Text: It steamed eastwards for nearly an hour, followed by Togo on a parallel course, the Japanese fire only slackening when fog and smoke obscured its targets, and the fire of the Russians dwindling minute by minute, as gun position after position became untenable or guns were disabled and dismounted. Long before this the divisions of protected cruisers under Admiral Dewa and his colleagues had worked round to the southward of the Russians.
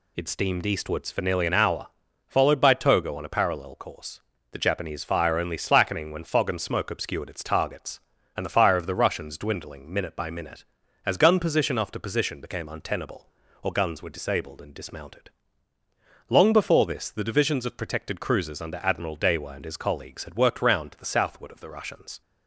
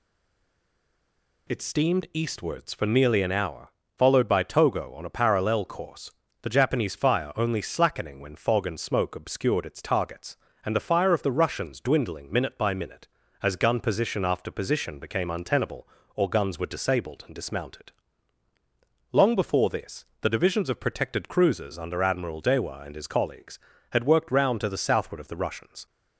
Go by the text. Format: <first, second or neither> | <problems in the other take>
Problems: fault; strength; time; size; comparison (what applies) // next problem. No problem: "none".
first | stays silent before the first word; noticeable; until 1.4 s; 1.4 s long // pauses between "this" and "the"; slight; at 20.0 s; 0.16 s long